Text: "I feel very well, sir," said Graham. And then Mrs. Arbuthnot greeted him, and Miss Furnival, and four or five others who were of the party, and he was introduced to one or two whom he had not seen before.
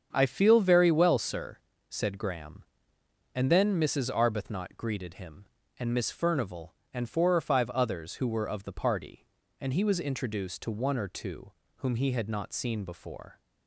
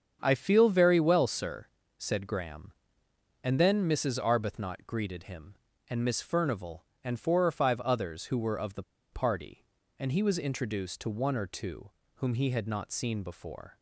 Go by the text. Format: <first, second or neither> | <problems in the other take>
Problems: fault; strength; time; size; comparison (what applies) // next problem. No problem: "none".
first | starts louder than the rest; strong; until 1.2 s; 7.5 dB; strong in the first // pauses between "the" and "party"; slight; at 8.8 s; 0.29 s long // pauses between "two" and "whom"; slight; at 11.9 s; 0.24 s long; slight in the first